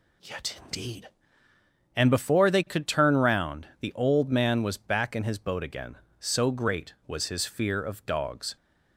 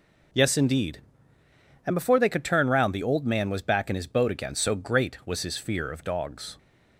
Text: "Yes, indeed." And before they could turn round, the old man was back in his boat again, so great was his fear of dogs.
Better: second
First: says "Yet" for "Yes"; at 0.2 s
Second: none

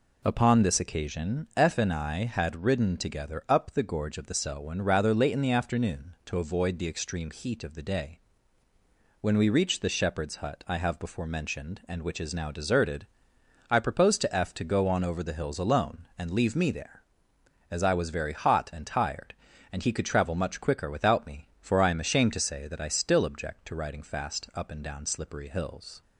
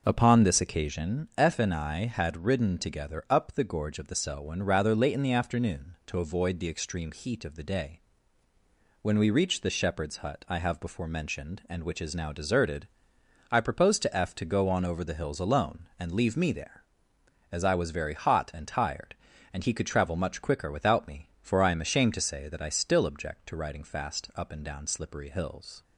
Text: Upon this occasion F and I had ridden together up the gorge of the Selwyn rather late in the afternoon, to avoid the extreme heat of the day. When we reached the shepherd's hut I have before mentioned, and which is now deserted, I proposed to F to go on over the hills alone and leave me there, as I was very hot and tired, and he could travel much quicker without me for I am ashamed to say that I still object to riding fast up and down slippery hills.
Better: first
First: none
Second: starts louder than the rest; noticeable; until 1.1 s; 6 dB

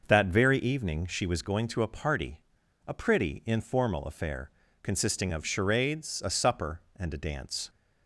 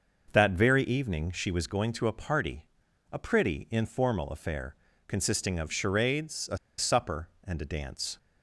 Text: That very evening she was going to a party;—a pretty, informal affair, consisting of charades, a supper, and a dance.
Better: first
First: starts louder than the rest; noticeable; until 1.0 s; 6 dB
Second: starts louder than the rest; noticeable; until 1.3 s; 6 dB // pauses between "a" and "supper"; slight; at 6.5 s; 0.21 s long

